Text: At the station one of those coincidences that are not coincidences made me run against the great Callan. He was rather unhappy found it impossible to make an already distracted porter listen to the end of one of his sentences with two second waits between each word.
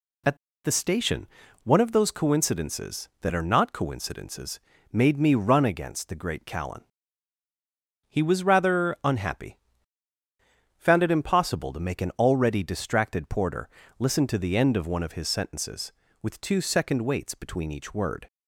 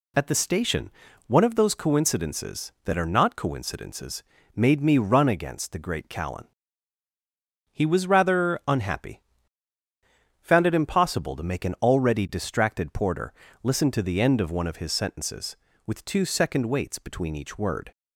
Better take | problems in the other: second | pauses between "At" and "the"; slight; at 0.3 s; 0.27 s long // pauses between "station" and "one"; slight; at 1.2 s; 0.36 s long; slight in the second // pauses between "coincidences" and "made"; slight; at 4.5 s; 0.32 s long; slight in the second // pauses between "unhappy" and "found"; at 9.5 s; 1.2 s long; also in the second // pauses between "porter" and "listen"; slight; at 13.6 s; 0.30 s long; slight in the second

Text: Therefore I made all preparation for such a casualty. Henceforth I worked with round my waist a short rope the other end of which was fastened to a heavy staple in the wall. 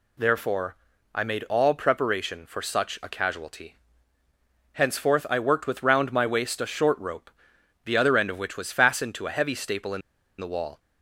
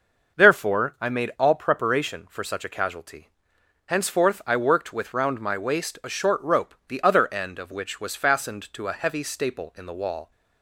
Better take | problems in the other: second | pauses between "Therefore" and "I"; at 0.7 s; 0.40 s long // pauses between "rope" and "the"; noticeable; at 7.3 s; 0.54 s long // pauses between "in" and "the"; at 10.0 s; 0.38 s long

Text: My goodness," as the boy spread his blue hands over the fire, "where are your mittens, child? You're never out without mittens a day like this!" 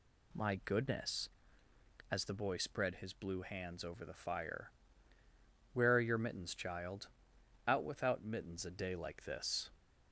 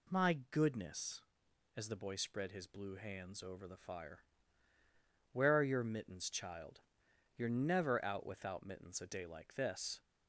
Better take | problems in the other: second | skips "You're never"; at 7.3 s

